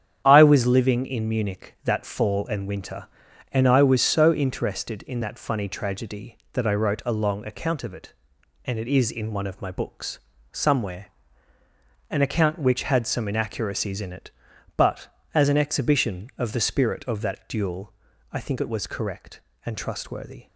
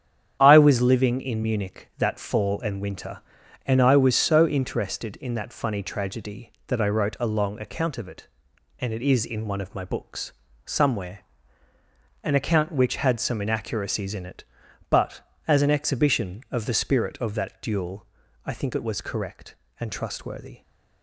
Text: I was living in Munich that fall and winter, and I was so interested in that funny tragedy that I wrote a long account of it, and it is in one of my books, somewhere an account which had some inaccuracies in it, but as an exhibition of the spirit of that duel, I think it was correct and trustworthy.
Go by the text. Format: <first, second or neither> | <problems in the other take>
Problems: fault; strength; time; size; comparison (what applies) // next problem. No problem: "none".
neither | starts louder than the rest; strong; the same in both // pauses between "somewhere" and "an"; the same in both